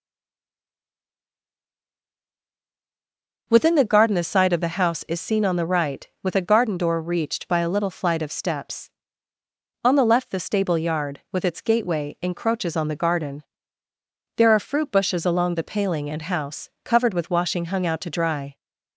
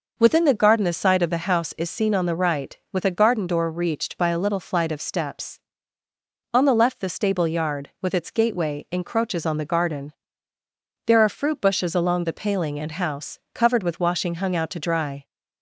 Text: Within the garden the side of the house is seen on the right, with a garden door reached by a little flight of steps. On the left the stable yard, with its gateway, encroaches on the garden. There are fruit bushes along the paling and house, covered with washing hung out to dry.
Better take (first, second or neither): second